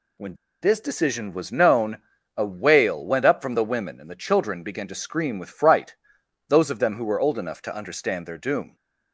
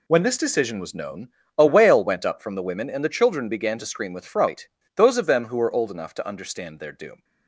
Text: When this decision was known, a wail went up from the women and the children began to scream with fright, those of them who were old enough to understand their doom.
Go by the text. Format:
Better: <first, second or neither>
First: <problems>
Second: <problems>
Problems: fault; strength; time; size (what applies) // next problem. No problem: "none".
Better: second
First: pauses between "When" and "this"; slight; at 0.3 s; 0.28 s long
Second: none